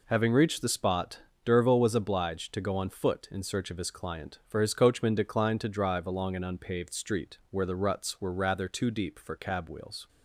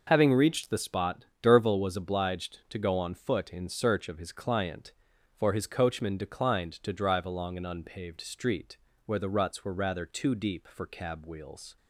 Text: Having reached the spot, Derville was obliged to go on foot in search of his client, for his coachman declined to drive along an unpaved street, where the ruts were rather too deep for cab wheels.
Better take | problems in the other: neither | none

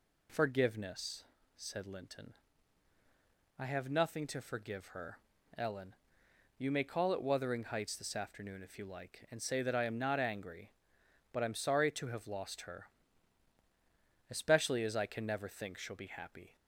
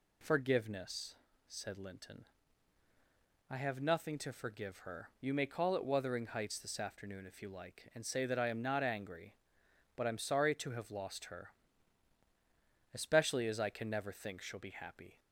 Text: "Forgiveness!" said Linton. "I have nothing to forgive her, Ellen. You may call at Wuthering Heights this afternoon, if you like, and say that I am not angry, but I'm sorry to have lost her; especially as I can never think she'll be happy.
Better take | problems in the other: first | skips "Ellen"; at 5.1 s

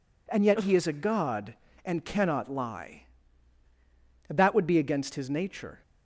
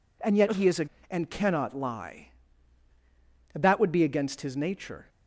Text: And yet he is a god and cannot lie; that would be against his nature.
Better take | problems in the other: first | skips "god"; at 0.9 s

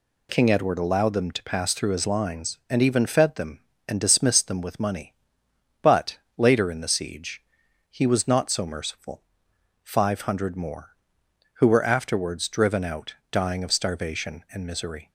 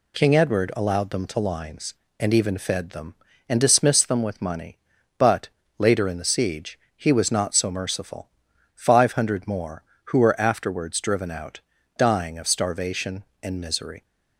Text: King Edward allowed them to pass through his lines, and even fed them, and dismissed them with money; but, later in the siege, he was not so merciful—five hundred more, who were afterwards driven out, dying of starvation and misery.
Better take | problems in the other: first | skips "pass through his"; at 1.3 s

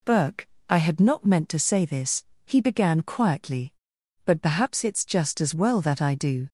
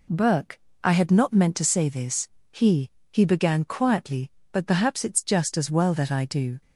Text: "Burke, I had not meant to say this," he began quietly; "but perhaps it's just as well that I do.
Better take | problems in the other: first | says "he" twice; at 3.1 s

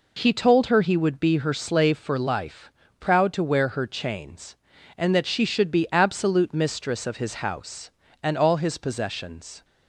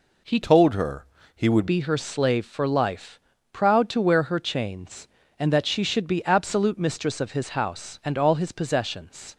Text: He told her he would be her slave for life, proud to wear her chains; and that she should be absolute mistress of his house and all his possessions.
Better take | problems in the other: first | changes voice from "told" to "would"; from 0.4 to 1.6 s; 1.2 s long // pauses between "her" and "he"; slight; at 1.0 s; 0.30 s long

